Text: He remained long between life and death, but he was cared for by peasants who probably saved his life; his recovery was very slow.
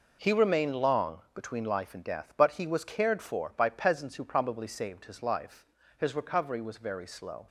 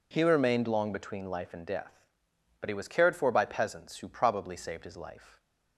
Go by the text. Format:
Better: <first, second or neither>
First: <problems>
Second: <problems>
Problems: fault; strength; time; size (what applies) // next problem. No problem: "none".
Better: first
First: none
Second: stops before "his recovery was very slow"; at 5.3 s